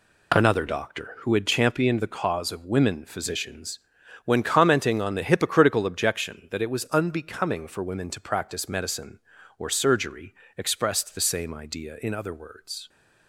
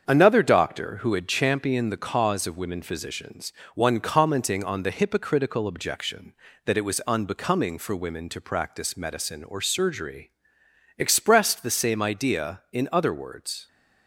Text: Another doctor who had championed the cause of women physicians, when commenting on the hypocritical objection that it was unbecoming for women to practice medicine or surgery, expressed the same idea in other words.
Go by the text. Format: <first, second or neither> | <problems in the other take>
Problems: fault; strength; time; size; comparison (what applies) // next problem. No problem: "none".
first | starts louder than the rest; strong; until 1.0 s; 7 dB // says "one" for "when"; at 3.7 s